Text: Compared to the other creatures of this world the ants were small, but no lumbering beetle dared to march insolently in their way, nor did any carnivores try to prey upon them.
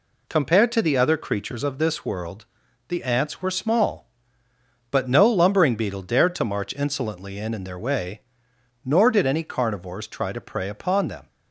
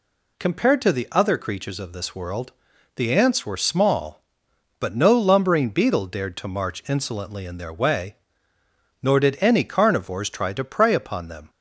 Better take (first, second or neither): second